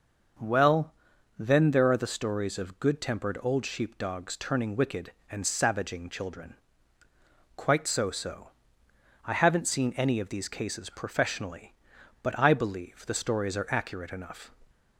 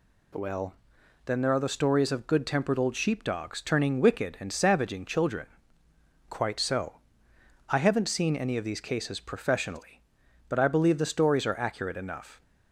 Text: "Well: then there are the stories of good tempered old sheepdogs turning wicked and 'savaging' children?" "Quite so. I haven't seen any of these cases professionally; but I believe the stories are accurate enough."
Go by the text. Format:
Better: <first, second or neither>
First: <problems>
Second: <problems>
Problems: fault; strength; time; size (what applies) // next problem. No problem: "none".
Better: second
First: starts louder than the rest; until 1.8 s; 6 dB // says "so" twice; at 8.1 s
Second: none